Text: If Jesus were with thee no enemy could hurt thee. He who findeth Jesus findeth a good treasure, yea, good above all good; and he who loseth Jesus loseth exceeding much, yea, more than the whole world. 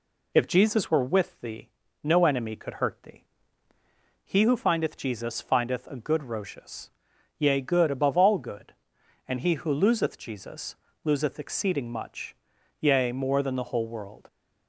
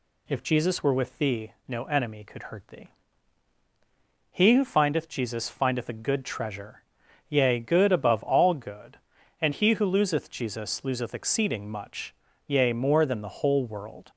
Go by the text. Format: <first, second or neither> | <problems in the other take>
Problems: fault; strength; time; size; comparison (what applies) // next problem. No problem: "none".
second | pauses between "thee" and "no"; slight; at 1.6 s; 0.32 s long; slight in the second // says "rocious" for "treasure"; at 6.2 s // pauses between "Jesus" and "loseth"; slight; at 10.7 s; 0.28 s long